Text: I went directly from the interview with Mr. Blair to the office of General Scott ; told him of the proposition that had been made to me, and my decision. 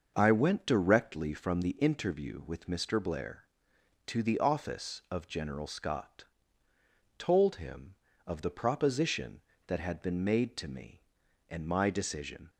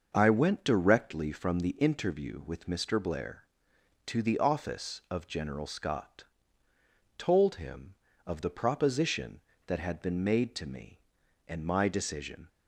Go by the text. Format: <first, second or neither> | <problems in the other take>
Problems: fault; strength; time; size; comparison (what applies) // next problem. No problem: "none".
neither | starts louder than the rest; noticeable; the same in both